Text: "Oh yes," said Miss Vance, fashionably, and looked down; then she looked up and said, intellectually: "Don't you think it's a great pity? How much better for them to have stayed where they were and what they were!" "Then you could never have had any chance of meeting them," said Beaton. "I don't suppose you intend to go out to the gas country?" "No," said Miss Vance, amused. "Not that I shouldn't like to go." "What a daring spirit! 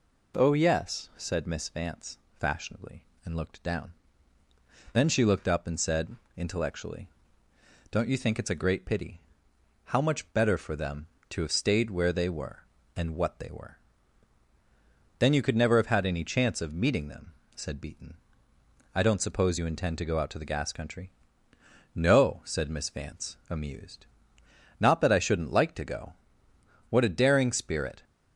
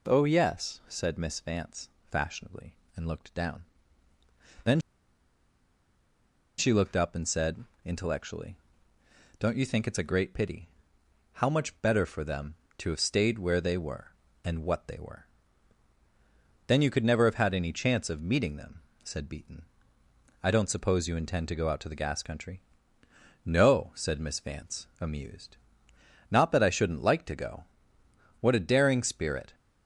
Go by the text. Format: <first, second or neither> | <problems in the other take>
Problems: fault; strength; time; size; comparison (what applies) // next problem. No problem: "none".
first | pauses between "then" and "she"; strong; at 4.7 s; 1.8 s long